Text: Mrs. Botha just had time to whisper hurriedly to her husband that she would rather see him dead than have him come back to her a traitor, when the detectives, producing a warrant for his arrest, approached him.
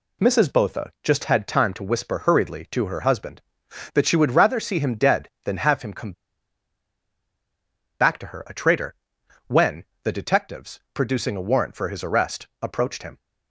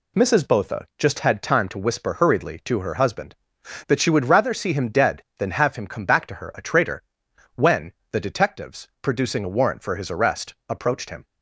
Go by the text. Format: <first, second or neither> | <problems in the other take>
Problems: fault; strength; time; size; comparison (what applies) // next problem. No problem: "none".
second | pauses between "come" and "back"; strong; at 6.1 s; 1.8 s long // pauses between "when" and "the"; slight; at 9.8 s; 0.20 s long; slight in the second